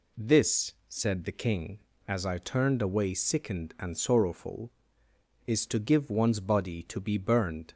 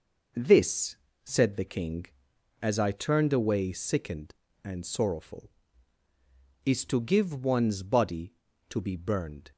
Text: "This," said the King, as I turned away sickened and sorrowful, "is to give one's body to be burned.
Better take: neither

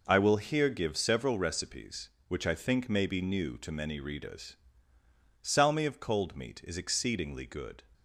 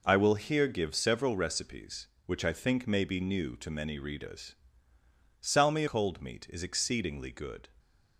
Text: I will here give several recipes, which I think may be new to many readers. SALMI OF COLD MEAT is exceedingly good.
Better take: first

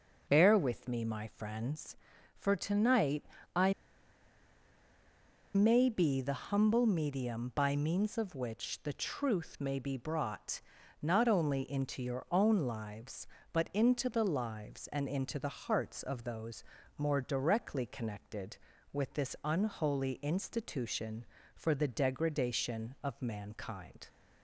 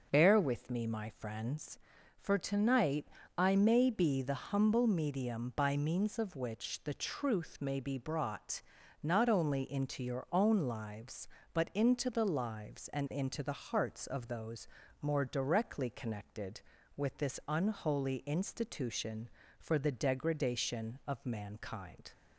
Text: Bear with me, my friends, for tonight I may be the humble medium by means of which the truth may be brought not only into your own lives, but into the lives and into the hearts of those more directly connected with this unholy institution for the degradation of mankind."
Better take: second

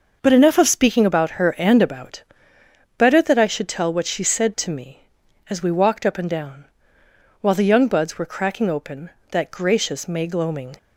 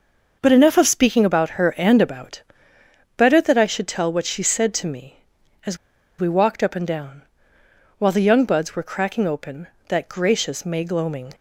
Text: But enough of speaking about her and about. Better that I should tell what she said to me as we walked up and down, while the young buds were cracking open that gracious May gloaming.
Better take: first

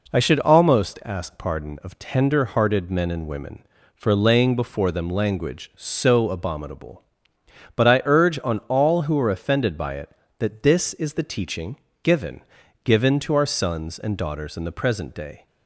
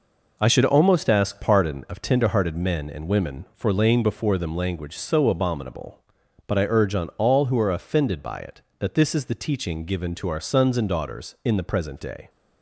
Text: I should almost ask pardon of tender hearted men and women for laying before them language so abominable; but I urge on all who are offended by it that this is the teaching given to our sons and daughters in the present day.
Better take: second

